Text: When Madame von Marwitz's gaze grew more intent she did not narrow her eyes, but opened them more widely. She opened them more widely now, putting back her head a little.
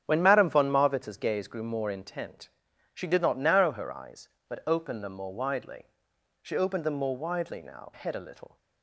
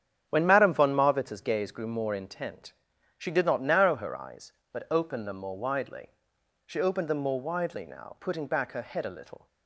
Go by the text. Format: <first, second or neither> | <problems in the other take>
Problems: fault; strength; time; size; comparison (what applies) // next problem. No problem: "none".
second | starts louder than the rest; strong; until 1.0 s; 9 dB; strong in the second // pauses between "intent" and "she"; at 2.4 s; 0.44 s long; also in the second // skips "putting back her"; at 7.9 s